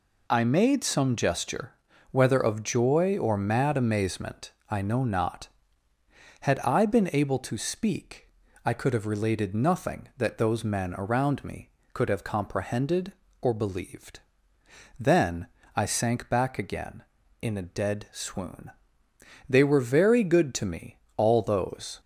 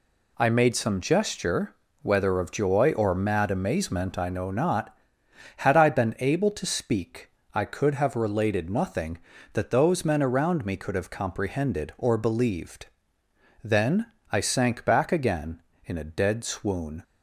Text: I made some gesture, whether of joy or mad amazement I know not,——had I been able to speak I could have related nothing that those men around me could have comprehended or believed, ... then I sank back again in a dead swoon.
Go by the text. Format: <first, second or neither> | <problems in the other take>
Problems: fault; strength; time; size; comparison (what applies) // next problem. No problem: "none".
second | pauses between "amazement" and "I"; slight; at 4.5 s; 0.18 s long // pauses between "speak" and "I"; slight; at 8.2 s; 0.34 s long; slight in the second // pauses between "then" and "I"; slight; at 15.4 s; 0.28 s long; slight in the second // goes on to say "They were very good to me all those"; strong; from 19.4 s on; 2.5 s long